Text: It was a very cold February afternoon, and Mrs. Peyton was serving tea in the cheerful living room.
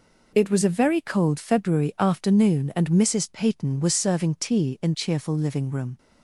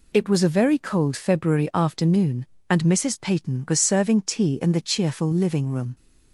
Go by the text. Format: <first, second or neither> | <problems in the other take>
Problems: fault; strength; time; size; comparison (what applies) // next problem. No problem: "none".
second | skips "the"; at 4.9 s